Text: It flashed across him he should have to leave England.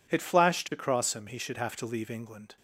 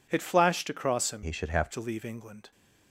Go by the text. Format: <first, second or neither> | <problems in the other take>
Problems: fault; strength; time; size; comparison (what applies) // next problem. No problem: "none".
first | changes voice from "he" to "have"; from 1.2 to 1.6 s; 0.4 s long